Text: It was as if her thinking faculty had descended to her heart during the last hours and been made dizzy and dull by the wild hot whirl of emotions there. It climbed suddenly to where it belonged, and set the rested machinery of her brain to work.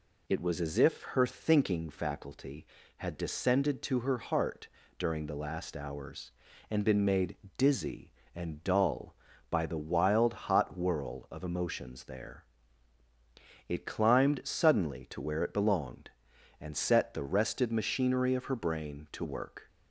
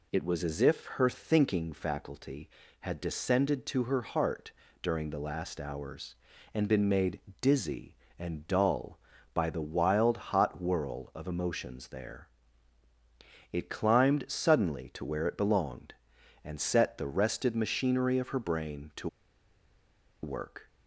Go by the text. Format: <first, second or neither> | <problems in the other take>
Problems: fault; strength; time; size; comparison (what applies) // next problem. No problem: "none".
first | pauses between "heart" and "during"; slight; at 4.5 s; 0.30 s long; slight in the first // pauses between "made" and "dizzy"; slight; at 7.1 s; 0.22 s long; slight in the first // pauses between "to" and "work"; at 19.0 s; 1.1 s long